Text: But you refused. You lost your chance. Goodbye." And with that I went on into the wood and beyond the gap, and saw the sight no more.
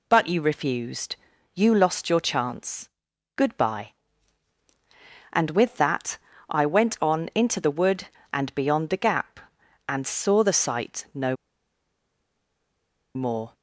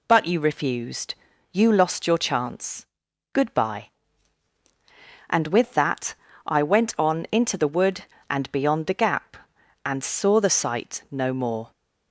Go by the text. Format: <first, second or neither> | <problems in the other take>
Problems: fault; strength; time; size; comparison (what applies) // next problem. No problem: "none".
second | pauses between "that" and "I"; slight; at 6.1 s; 0.32 s long; slight in the second // pauses between "no" and "more"; strong; at 11.3 s; 1.7 s long